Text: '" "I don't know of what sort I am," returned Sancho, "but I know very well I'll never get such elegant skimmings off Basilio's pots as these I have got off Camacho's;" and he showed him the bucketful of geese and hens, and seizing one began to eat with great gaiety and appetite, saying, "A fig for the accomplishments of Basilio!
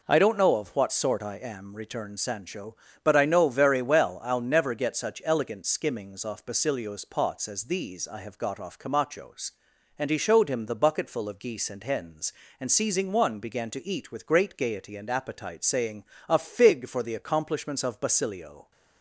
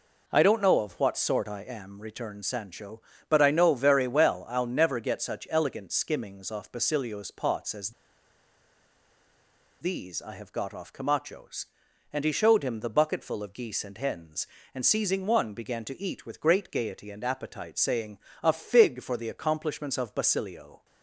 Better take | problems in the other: first | pauses between "as" and "these"; strong; at 7.9 s; 1.9 s long

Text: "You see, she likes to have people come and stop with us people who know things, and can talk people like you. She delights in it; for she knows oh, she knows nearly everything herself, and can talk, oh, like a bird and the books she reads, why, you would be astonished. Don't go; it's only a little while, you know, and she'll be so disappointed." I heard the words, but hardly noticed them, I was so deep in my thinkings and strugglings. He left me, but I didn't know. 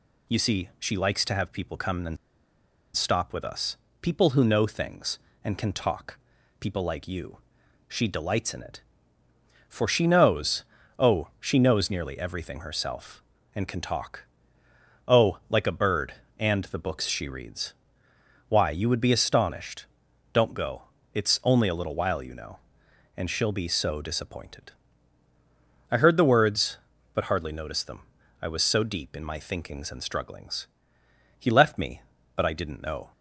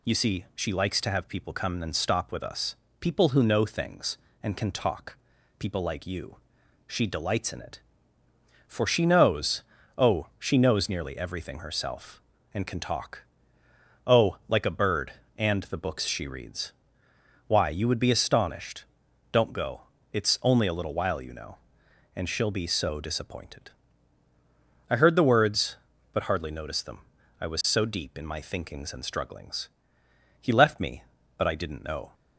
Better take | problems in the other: second | pauses between "and" and "stop"; noticeable; at 2.1 s; 0.78 s long // pauses between "us" and "people"; slight; at 3.7 s; 0.26 s long; slight in the second // pauses between "talk" and "people"; at 6.1 s; 0.42 s long; also in the second // pauses between "knows" and "oh"; slight; at 10.6 s; 0.36 s long; slight in the second

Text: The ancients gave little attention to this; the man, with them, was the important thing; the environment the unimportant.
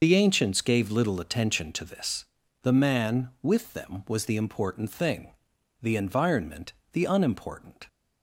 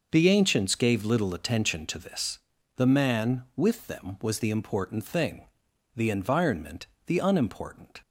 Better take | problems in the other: second | loses the start of "The"; at 0.0 s; 45 ms // starts louder than the rest; noticeable; until 1.0 s; 6 dB // pauses between "environment" and "the"; slight; at 6.7 s; 0.18 s long; slight in the second

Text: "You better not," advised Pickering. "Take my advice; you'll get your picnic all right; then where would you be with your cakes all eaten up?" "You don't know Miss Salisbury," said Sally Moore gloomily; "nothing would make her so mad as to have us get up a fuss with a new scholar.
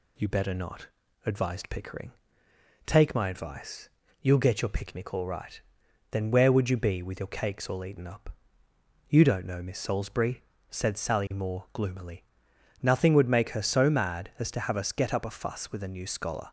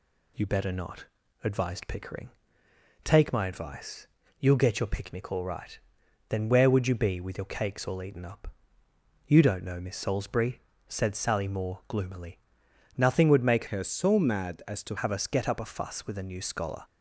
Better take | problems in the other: first | changes voice from "her" to "to"; from 13.6 to 14.9 s; 1.3 s long

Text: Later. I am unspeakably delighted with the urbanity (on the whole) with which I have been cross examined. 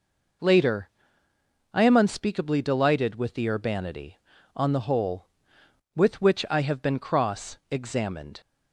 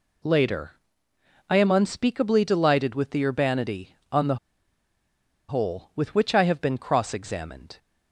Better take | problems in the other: first | pauses between "the" and "whole"; at 4.3 s; 1.1 s long

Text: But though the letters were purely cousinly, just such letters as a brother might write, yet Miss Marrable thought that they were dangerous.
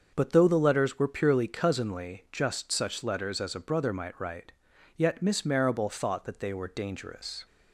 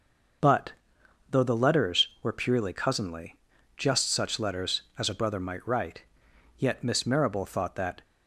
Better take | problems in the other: first | starts louder than the rest; noticeable; until 2.0 s; 6 dB; also in the first // pauses between "But" and "though"; noticeable; at 0.7 s; 0.58 s long // stops before "they were dangerous"; at 8.0 s

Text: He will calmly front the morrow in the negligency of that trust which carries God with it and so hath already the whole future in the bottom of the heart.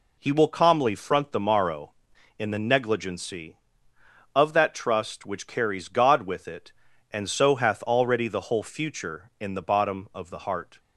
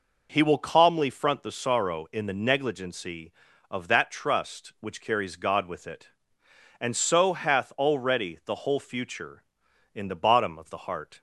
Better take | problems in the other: first | says "sorrow" for "morrow"; at 1.5 s

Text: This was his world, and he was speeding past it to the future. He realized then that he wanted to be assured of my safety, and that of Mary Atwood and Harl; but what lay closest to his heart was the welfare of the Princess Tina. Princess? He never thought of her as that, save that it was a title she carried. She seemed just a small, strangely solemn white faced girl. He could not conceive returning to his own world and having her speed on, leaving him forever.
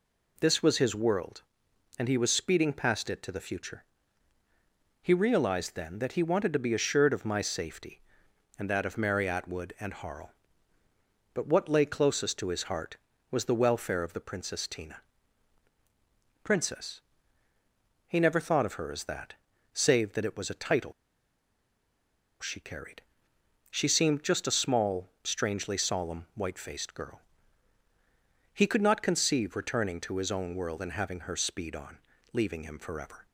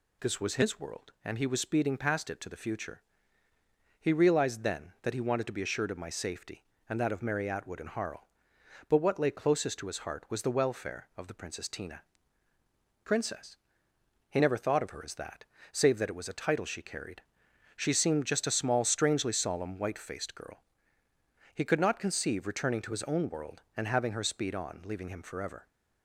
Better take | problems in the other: second | pauses between "title" and "she"; strong; at 20.9 s; 1.4 s long

